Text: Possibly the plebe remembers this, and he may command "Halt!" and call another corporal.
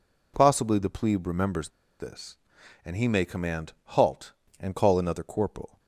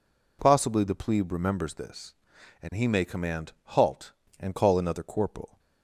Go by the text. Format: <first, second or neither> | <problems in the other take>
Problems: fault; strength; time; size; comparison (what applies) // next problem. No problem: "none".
second | pauses between "remembers" and "this"; slight; at 1.6 s; 0.30 s long